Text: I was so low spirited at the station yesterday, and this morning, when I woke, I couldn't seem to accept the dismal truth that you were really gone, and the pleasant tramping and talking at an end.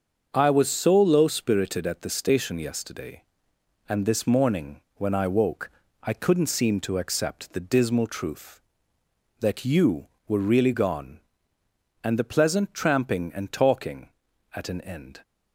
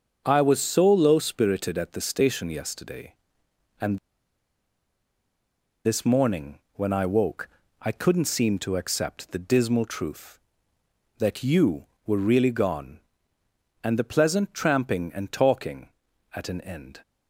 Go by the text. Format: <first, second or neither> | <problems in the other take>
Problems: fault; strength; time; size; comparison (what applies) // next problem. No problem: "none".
first | starts louder than the rest; until 1.2 s; 7 dB; also in the first // pauses between "and" and "this"; strong; at 3.9 s; 1.8 s long